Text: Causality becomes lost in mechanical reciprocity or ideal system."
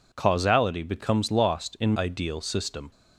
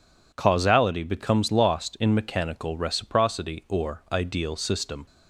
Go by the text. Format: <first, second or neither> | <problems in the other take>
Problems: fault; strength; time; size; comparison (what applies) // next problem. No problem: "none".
second | skips "mechanical reciprocity or"; at 1.9 s